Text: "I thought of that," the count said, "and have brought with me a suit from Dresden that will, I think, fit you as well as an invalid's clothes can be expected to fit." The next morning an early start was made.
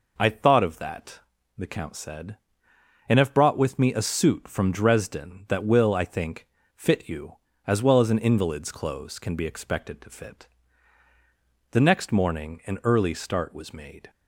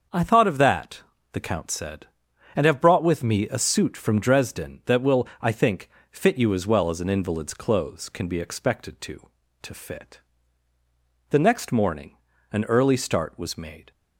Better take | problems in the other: first | starts louder than the rest; until 1.4 s; 6.5 dB // says "to" twice; at 9.6 s // pauses between "morning" and "an"; slight; at 12.1 s; 0.34 s long

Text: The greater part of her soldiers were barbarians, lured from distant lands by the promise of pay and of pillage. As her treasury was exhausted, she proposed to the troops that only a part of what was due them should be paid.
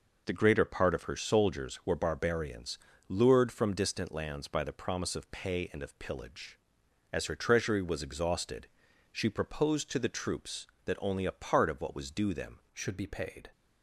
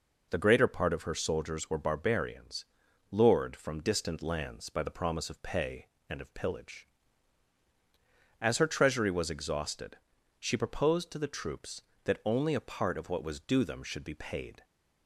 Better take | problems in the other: second | changes voice at "should"; from 12.7 s on; 0.7 s long

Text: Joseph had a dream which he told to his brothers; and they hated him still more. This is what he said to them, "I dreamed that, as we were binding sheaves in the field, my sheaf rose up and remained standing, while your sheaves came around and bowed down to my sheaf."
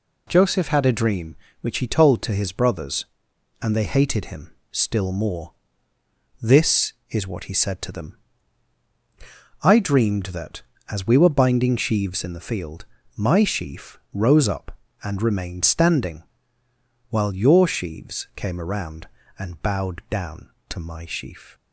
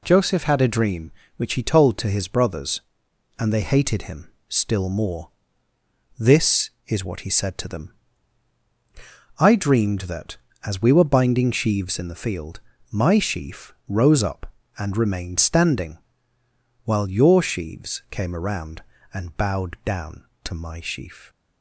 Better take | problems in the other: neither | pauses between "him" and "still"; slight; the same in both

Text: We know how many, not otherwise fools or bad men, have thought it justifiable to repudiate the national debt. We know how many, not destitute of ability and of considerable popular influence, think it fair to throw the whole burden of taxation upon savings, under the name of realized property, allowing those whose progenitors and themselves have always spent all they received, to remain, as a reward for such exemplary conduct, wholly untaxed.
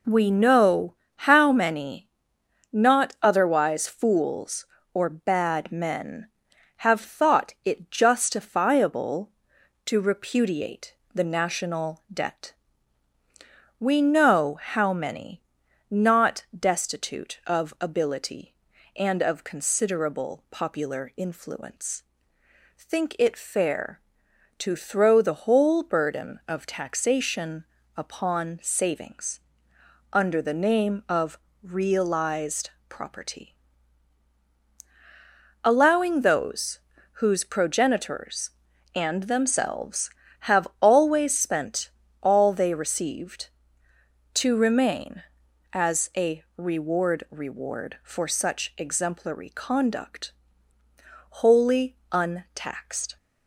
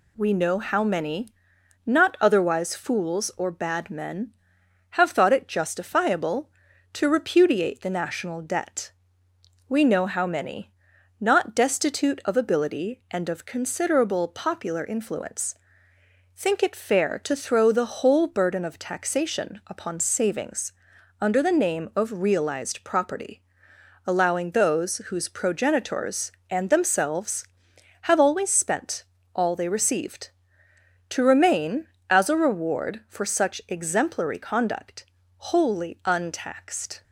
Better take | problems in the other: second | pauses between "know" and "how"; slight; at 0.9 s; 0.22 s long // pauses between "repudiate" and "the"; slight; at 10.9 s; 0.18 s long // pauses between "taxation" and "upon"; slight; at 27.6 s; 0.32 s long // pauses between "of" and "realized"; slight; at 31.3 s; 0.26 s long // pauses between "realized" and "property"; slight; at 32.7 s; 0.18 s long // pauses between "those" and "whose"; slight; at 36.7 s; 0.36 s long // pauses between "spent" and "all"; slight; at 41.9 s; 0.32 s long; slight in the second // says "reward" twice; at 47.2 s // pauses between "wholly" and "untaxed"; slight; at 51.9 s; 0.16 s long

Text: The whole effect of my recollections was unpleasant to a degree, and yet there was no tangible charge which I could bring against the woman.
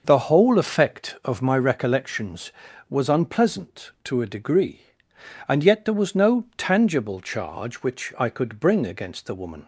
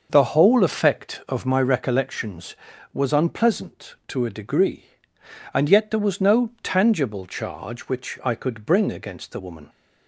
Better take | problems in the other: neither | none

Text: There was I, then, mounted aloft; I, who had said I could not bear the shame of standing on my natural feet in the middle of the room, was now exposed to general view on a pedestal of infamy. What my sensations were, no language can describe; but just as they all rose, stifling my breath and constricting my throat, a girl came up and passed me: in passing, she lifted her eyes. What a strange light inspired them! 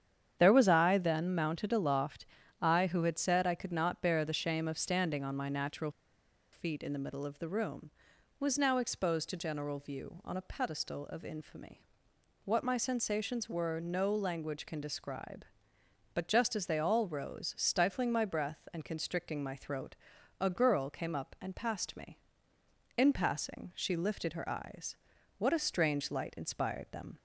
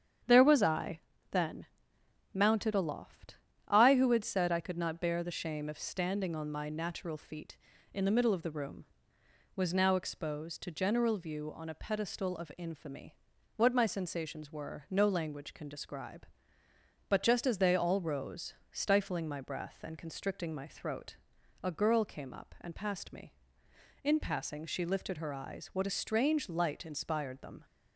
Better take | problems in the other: second | starts louder than the rest; strong; until 1.3 s; 8.5 dB; strong in the second // pauses between "natural" and "feet"; noticeable; at 5.9 s; 0.61 s long

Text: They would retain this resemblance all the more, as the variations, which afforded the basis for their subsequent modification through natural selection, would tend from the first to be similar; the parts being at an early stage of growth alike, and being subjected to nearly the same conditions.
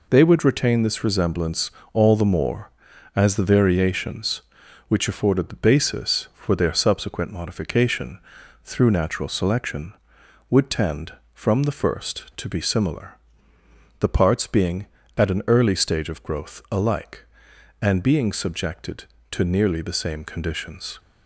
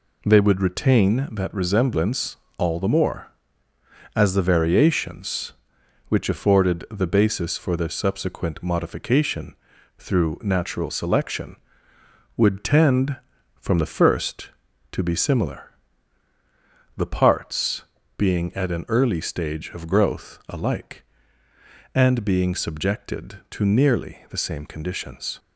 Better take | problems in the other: first | says "that" for "this"; at 1.3 s // pauses between "resemblance" and "all"; slight; at 2.3 s; 0.22 s long; slight in the first // pauses between "modification" and "through"; at 9.5 s; 0.42 s long; also in the first // pauses between "parts" and "being"; slight; at 17.8 s; 0.34 s long

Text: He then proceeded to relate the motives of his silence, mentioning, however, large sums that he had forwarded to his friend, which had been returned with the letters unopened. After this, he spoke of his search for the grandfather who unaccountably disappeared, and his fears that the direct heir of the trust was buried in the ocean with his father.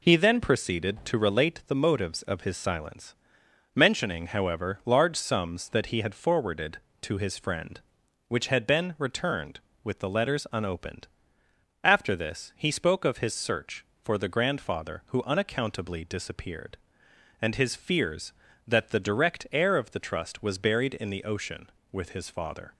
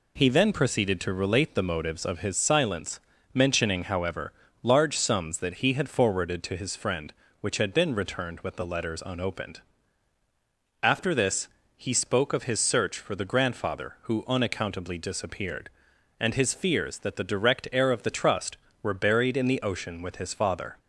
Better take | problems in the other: first | says "were" for "was"; at 18.8 s

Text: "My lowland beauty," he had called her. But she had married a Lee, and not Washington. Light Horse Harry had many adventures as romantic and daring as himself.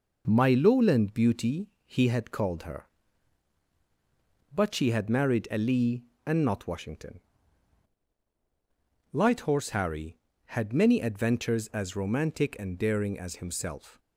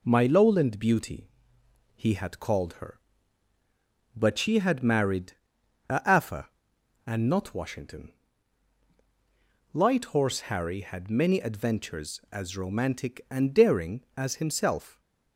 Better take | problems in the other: first | pauses between "married" and "a"; noticeable; at 5.3 s; 0.56 s long // says "Afa" for "Lee"; at 6.0 s

